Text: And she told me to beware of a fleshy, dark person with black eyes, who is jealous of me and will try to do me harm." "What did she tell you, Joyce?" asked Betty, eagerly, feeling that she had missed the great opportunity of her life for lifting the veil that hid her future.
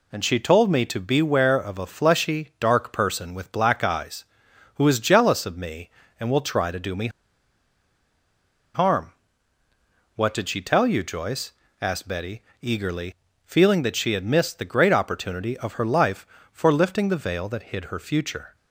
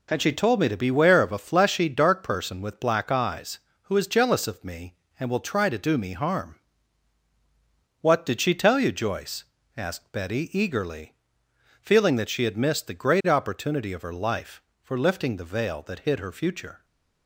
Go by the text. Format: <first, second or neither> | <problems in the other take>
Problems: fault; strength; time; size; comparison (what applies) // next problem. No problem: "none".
second | pauses between "me" and "harm"; strong; at 7.0 s; 1.6 s long